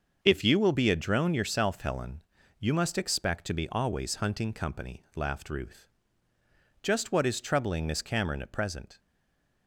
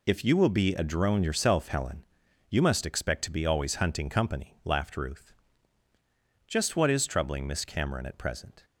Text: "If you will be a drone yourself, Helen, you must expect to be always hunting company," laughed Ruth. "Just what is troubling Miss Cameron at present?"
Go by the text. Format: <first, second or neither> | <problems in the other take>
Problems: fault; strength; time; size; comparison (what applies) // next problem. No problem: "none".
second | starts louder than the rest; until 1.2 s; 6.5 dB // stays silent after the last word; slight; from 8.9 s on; 0.7 s long